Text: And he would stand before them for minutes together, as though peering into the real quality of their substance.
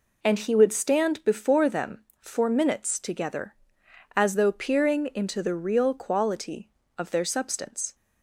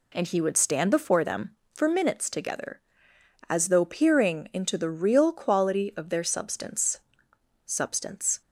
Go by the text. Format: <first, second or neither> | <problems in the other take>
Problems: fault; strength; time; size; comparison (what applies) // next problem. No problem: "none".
first | says "substance" twice; at 7.6 s